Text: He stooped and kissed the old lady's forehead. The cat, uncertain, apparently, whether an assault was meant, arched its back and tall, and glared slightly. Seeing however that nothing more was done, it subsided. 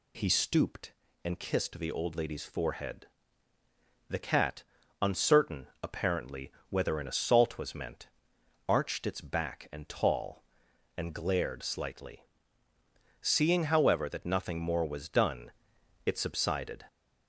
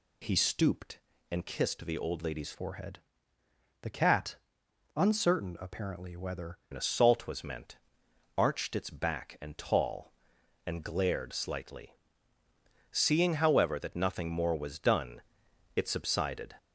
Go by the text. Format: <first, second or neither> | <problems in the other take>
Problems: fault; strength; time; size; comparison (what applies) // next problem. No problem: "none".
first | changes voice from "forehead" to "whether"; from 2.5 to 6.5 s; 4.0 s long